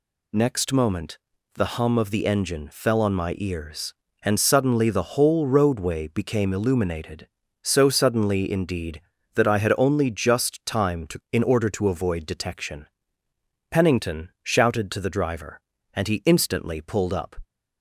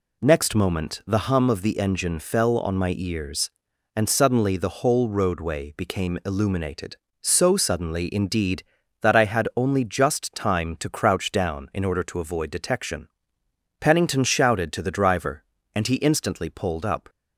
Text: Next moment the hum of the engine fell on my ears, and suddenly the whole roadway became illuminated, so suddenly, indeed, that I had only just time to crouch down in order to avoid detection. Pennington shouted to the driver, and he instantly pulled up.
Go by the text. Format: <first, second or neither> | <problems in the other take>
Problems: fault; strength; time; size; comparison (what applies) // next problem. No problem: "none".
second | pauses between "moment" and "the"; slight; at 1.1 s; 0.36 s long // skips "crouch down"; at 11.2 s